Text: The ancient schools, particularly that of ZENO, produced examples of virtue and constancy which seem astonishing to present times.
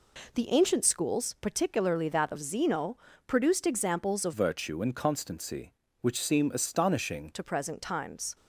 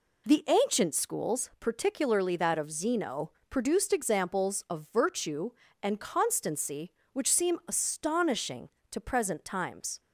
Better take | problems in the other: second | changes voice from "virtue" to "astonishing"; from 4.3 to 7.3 s; 3.0 s long

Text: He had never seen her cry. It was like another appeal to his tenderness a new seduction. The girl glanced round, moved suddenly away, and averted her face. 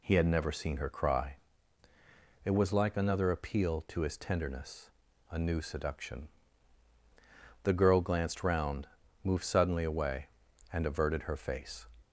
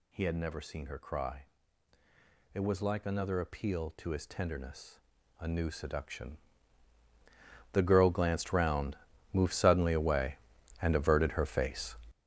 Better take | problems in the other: first | gets louder; strong; throughout; 10.5 dB // pauses between "tenderness" and "a"; at 4.9 s; 0.42 s long; also in the first

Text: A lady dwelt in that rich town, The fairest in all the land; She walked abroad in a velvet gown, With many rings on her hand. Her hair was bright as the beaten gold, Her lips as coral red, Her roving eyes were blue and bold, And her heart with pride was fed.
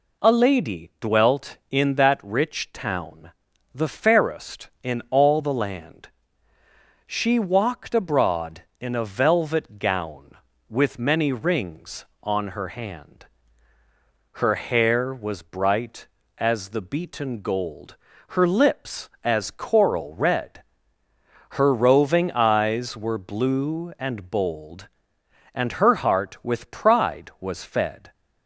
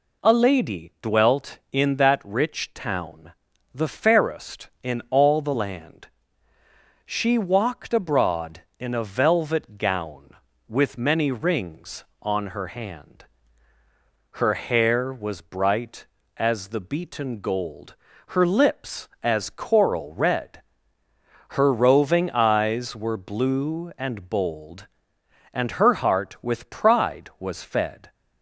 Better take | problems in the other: neither | none

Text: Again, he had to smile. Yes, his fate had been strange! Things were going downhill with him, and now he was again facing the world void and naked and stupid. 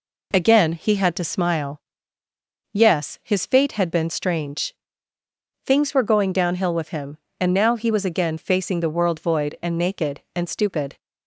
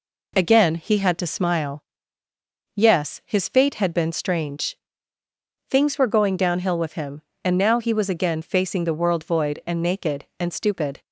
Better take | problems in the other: neither | none

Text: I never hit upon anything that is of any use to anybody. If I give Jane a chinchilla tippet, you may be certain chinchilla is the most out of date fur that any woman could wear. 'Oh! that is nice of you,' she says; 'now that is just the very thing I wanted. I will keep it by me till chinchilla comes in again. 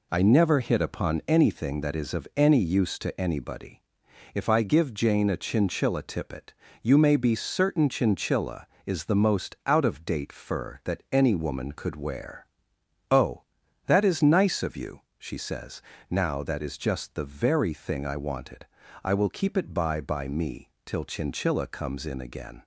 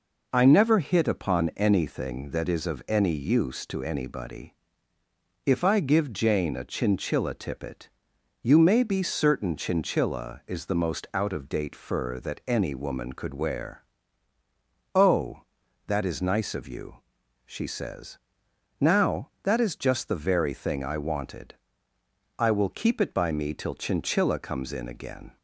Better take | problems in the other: second | says "by" twice; at 20.0 s // pauses between "me" and "till"; slight; at 20.7 s; 0.16 s long

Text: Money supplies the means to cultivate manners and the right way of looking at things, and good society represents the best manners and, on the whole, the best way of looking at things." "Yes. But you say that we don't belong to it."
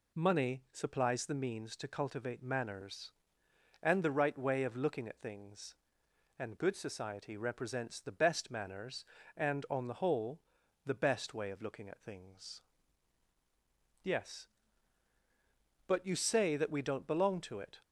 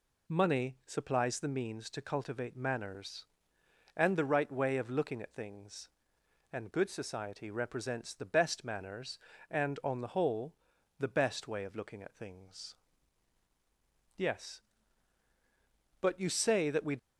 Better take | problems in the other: first | stops before "don't belong to it"; at 16.9 s

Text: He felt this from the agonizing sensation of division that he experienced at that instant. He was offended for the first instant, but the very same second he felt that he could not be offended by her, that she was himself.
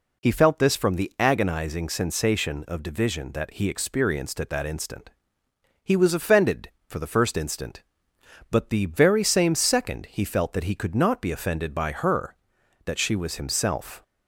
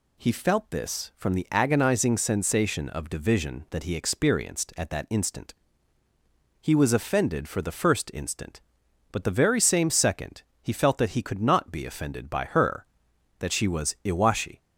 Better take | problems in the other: first | pauses between "second" and "he"; slight; at 10.4 s; 0.18 s long // says "iwashi" for "himself"; at 14.0 s

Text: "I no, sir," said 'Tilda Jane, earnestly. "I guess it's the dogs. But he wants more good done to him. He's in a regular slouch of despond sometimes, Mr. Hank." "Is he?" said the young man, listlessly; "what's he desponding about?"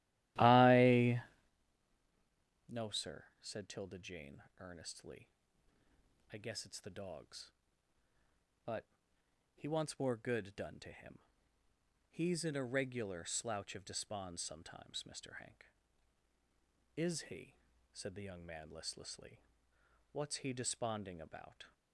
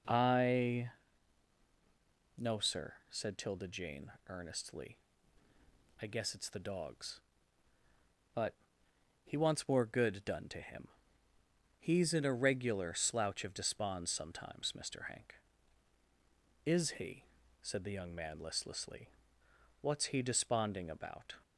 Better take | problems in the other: second | starts louder than the rest; strong; until 1.6 s; 14.5 dB // pauses between "I" and "no"; strong; at 1.2 s; 1.4 s long; strong in the second // pauses between "But" and "he"; noticeable; at 8.8 s; 0.70 s long; noticeable in the second

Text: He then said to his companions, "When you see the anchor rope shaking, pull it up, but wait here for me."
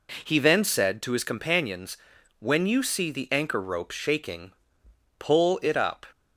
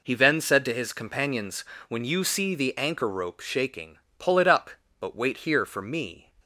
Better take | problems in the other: second | stops before "but wait here for me"; at 6.1 s

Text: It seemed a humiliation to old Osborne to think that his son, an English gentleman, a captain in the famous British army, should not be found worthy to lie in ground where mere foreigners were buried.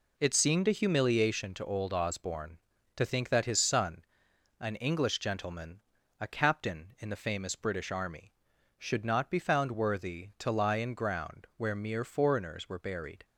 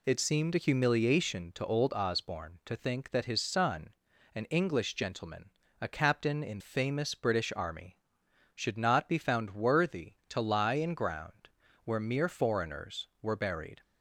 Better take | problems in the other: first | skips "the"; at 6.6 s // pauses between "ground" and "where"; slight; at 11.4 s; 0.36 s long

